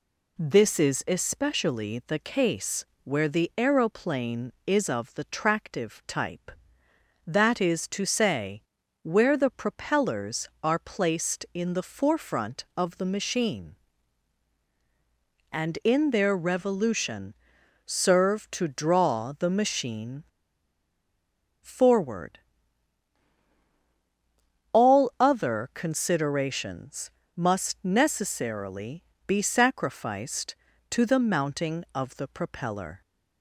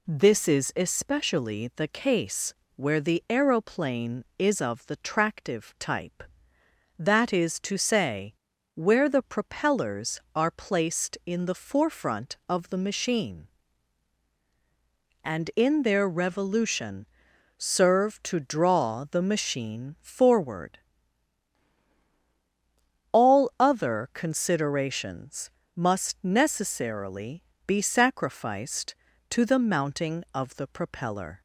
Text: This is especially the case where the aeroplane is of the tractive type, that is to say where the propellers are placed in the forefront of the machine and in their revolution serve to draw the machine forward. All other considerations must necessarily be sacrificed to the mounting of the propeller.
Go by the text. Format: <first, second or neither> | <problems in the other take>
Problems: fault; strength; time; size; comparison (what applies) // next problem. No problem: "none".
second | pauses between "case" and "where"; slight; at 2.8 s; 0.20 s long; slight in the second // pauses between "say" and "where"; at 8.6 s; 0.42 s long; also in the second // pauses between "revolution" and "serve"; noticeable; at 17.3 s; 0.54 s long; noticeable in the second // pauses between "machine" and "forward"; strong; at 20.2 s; 1.3 s long // pauses between "considerations" and "must"; slight; at 27.1 s; 0.24 s long; slight in the second // pauses between "necessarily" and "be"; slight; at 29.0 s; 0.24 s long; slight in the second